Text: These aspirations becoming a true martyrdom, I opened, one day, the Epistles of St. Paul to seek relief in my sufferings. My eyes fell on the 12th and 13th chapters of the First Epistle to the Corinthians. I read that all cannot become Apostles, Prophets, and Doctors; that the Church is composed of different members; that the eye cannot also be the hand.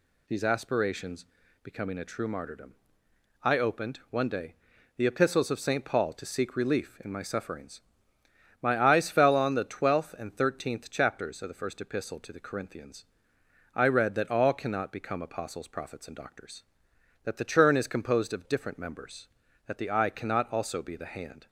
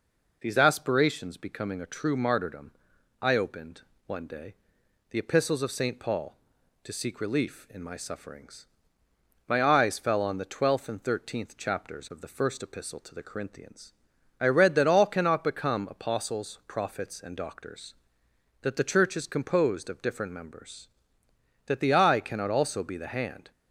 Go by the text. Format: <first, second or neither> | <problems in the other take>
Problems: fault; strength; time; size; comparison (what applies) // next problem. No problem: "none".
second | pauses between "aspirations" and "becoming"; at 1.2 s; 0.38 s long // says "Churn" for "Church"; at 17.4 s